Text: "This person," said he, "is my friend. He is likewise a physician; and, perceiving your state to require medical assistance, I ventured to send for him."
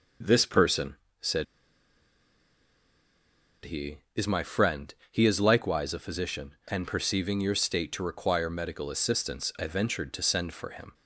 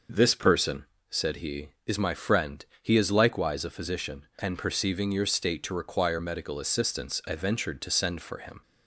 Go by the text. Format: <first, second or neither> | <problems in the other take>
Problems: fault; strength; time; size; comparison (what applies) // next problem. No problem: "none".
second | pauses between "said" and "he"; strong; at 1.4 s; 2.2 s long